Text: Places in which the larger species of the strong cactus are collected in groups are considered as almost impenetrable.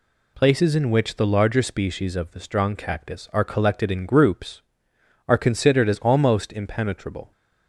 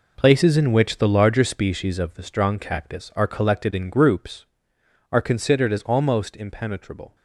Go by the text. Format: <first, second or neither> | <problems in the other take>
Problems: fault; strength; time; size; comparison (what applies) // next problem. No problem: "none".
first | gets quieter; strong; throughout; 11 dB